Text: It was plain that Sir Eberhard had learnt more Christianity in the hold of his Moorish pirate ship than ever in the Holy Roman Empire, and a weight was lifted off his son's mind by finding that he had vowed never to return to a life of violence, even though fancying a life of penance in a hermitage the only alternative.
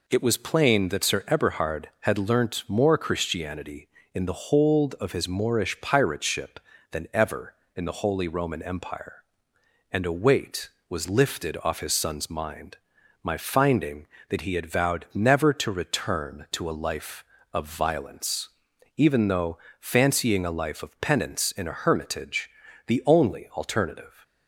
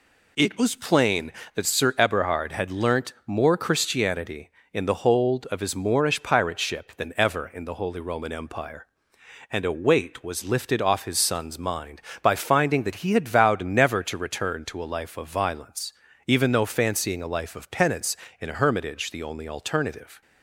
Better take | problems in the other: second | says "my" for "by"; at 13.2 s // pauses between "though" and "fancying"; slight; at 19.5 s; 0.24 s long // pauses between "hermitage" and "the"; at 22.4 s; 0.38 s long

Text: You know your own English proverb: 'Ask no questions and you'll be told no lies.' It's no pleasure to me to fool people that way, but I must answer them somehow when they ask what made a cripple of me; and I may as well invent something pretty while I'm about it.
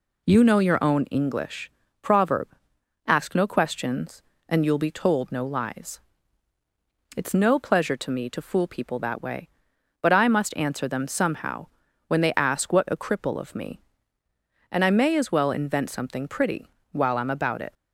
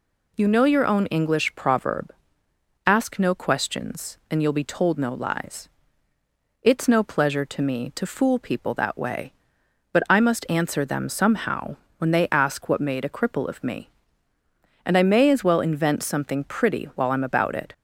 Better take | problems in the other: second | pauses between "English" and "proverb"; slight; at 1.7 s; 0.32 s long // pauses between "somehow" and "when"; at 11.6 s; 0.40 s long; slight in the second // skips "made"; at 12.8 s // pauses between "pretty" and "while"; slight; at 16.6 s; 0.24 s long

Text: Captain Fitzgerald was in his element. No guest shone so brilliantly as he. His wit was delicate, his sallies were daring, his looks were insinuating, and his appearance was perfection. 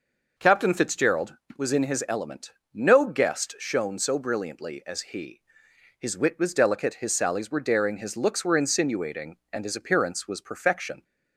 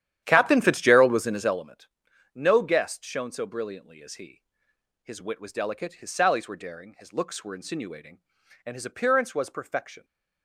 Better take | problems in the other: first | starts louder than the rest; strong; until 1.7 s; 11 dB

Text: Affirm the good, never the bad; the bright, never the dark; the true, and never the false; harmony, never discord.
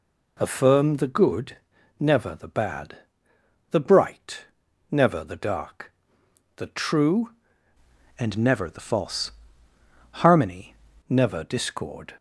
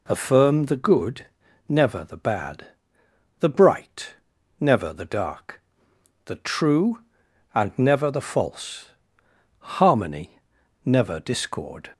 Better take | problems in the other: second | changes voice from "and" to "harmony"; from 8.1 to 10.7 s; 2.6 s long

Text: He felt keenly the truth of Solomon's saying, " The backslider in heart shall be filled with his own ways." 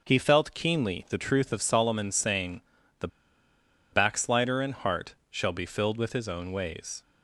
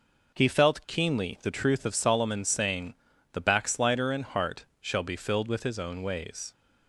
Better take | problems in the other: second | pauses between "The" and "backslider"; noticeable; at 3.0 s; 0.85 s long // pauses between "heart" and "shall"; slight; at 5.1 s; 0.16 s long; slight in the second

